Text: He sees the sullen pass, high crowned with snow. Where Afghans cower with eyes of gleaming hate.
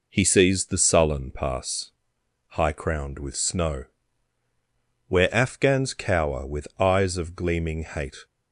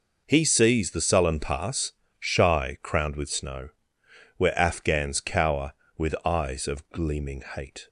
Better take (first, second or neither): first